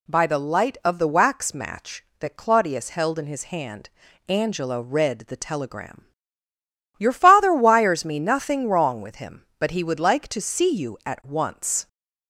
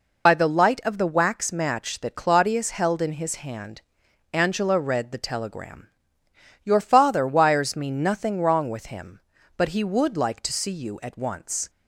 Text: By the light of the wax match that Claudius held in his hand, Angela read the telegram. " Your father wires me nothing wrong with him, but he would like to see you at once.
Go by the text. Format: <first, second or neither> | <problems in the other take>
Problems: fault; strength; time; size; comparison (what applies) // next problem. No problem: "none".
first | loses the start of "By"; at 0.2 s; 65 ms